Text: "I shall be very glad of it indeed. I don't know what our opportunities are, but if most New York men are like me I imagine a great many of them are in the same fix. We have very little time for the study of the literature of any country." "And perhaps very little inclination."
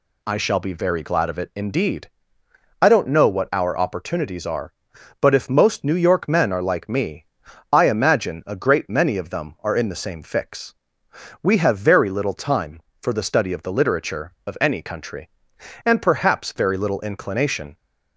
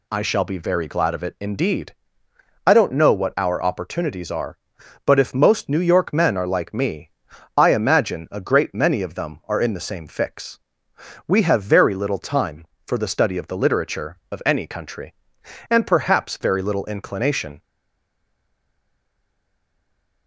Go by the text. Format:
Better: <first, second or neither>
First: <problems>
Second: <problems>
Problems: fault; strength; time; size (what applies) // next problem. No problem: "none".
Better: first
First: pauses between "me" and "I"; noticeable; at 7.2 s; 0.46 s long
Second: pauses between "me" and "I"; noticeable; at 7.1 s; 0.46 s long // stays silent after the last word; strong; from 17.6 s on; 2.6 s long